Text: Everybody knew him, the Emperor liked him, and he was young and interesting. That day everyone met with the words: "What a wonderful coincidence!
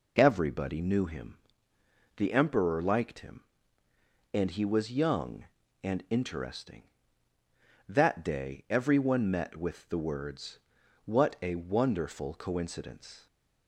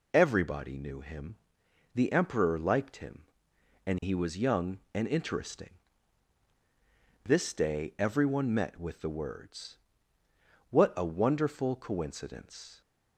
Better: first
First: none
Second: says "This" for "That"; at 7.2 s

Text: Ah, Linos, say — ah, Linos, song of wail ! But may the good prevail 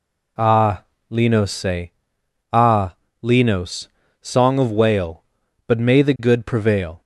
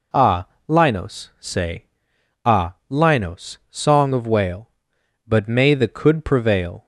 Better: first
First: none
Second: says "could" for "good"; at 5.8 s

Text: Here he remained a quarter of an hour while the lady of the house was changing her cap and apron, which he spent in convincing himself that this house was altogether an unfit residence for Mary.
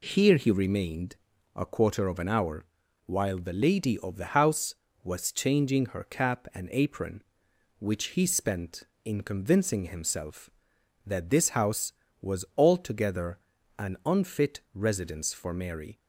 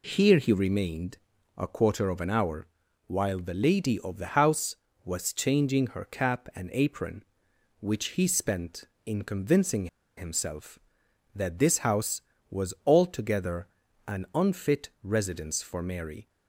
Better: first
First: pauses between "remained" and "a"; at 1.1 s; 0.40 s long // pauses between "hour" and "while"; at 2.6 s; 0.40 s long // pauses between "altogether" and "an"; at 13.3 s; 0.40 s long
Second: pauses between "remained" and "a"; at 1.1 s; 0.40 s long // pauses between "hour" and "while"; at 2.6 s; 0.40 s long // pauses between "convincing" and "himself"; slight; at 9.8 s; 0.30 s long // pauses between "altogether" and "an"; at 13.6 s; 0.40 s long

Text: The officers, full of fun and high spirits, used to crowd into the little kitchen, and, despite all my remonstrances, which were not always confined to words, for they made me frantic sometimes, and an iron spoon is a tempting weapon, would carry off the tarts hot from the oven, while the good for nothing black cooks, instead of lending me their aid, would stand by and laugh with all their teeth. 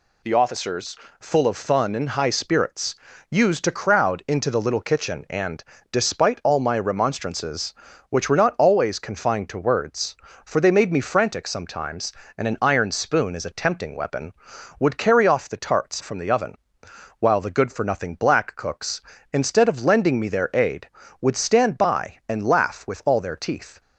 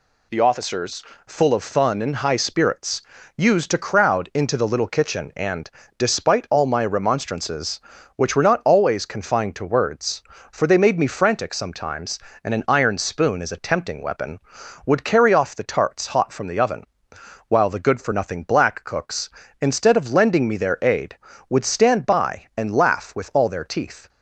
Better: second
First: skips "hot"; at 16.0 s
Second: none

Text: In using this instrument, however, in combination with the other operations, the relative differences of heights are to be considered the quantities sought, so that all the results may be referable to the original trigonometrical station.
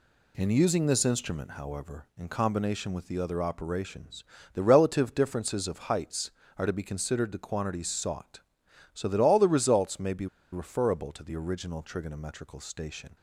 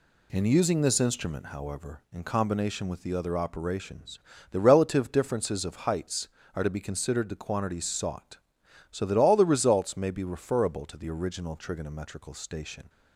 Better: second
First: pauses between "be" and "referable"; slight; at 10.2 s; 0.26 s long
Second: none

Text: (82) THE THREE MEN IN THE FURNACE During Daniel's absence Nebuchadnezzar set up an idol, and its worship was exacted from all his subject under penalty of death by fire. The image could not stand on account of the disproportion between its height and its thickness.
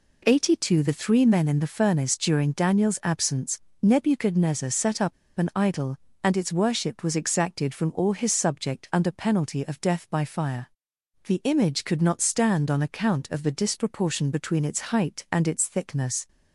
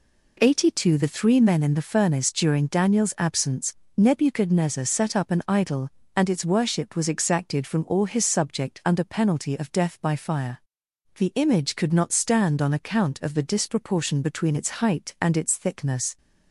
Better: second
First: pauses between "absence" and "Nebuchadnezzar"; slight; at 3.5 s; 0.22 s long // pauses between "up" and "an"; slight; at 5.1 s; 0.25 s long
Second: pauses between "absence" and "Nebuchadnezzar"; slight; at 3.7 s; 0.22 s long

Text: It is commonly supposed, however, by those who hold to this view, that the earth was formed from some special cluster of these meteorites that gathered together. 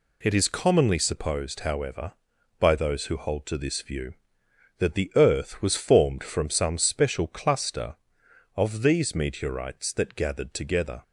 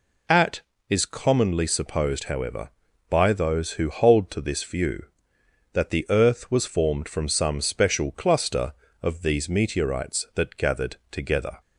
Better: first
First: none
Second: says "At" for "It"; at 0.2 s

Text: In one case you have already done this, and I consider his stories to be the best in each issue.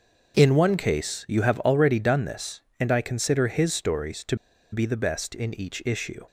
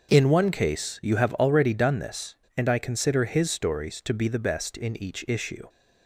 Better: second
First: starts louder than the rest; noticeable; until 1.4 s; 6 dB // pauses between "to" and "be"; at 4.3 s; 0.36 s long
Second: starts louder than the rest; noticeable; until 1.1 s; 6 dB

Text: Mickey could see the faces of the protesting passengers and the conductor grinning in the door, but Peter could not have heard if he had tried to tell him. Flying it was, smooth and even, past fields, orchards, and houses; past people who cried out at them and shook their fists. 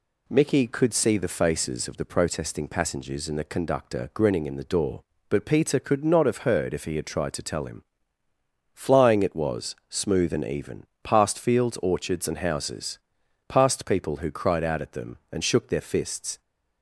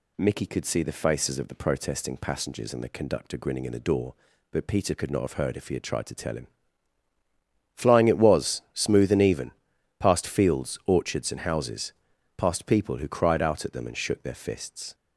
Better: neither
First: none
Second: none

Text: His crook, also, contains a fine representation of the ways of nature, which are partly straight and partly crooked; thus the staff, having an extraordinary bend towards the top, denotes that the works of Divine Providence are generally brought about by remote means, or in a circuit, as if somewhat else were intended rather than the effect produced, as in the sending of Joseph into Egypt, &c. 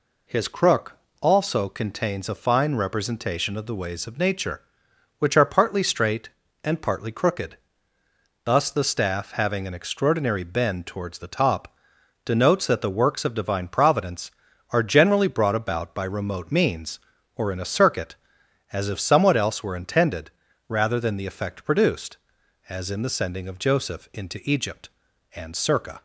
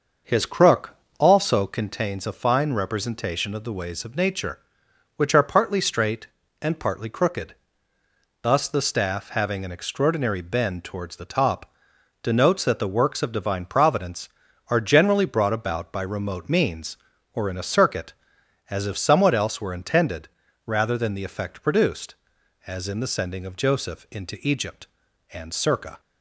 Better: first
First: pauses between "intended" and "rather"; at 20.2 s; 0.38 s long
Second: starts louder than the rest; noticeable; until 1.9 s; 6 dB // pauses between "intended" and "rather"; at 20.2 s; 0.38 s long

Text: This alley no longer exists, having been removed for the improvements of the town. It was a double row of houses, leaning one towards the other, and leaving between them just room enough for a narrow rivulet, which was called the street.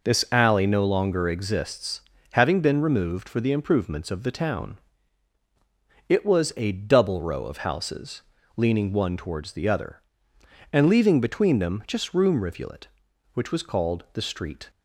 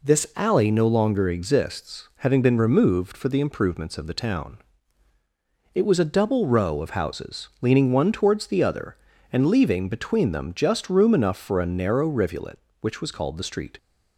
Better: second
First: skips "enough for a narrow"; at 12.4 s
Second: none

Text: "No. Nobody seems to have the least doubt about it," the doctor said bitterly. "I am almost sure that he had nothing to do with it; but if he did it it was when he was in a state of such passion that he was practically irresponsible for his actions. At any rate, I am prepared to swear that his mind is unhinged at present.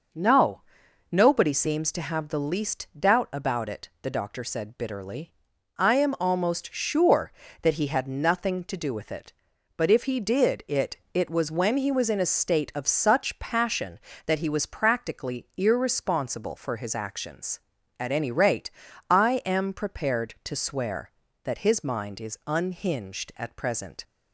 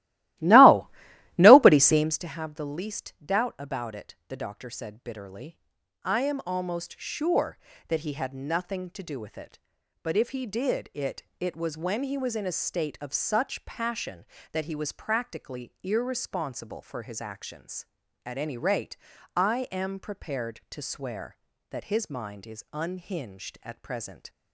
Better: first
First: pauses between "it" and "it"; slight; at 10.9 s; 0.16 s long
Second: starts louder than the rest; strong; until 2.3 s; 16.5 dB // pauses between "it" and "it"; slight; at 11.2 s; 0.16 s long

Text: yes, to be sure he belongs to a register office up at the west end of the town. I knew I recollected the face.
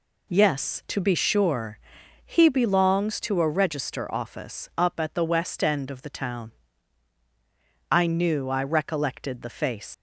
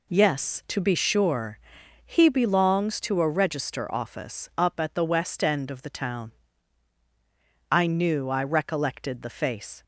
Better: second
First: pauses between "sure" and "he"; noticeable; at 1.7 s; 0.46 s long // leaves "face" unfinished; at 9.9 s; 85 ms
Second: pauses between "sure" and "he"; noticeable; at 1.5 s; 0.46 s long

